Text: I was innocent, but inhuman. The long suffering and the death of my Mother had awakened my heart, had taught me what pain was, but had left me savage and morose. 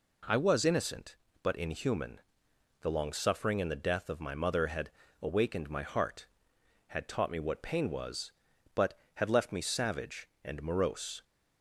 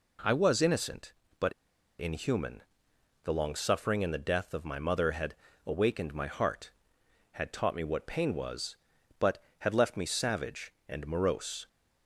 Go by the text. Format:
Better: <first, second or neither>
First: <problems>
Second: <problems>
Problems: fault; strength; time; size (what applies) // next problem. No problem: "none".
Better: first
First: pauses between "had" and "awakened"; slight; at 4.9 s; 0.28 s long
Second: pauses between "but" and "inhuman"; noticeable; at 1.5 s; 0.46 s long // pauses between "had" and "awakened"; slight; at 5.3 s; 0.28 s long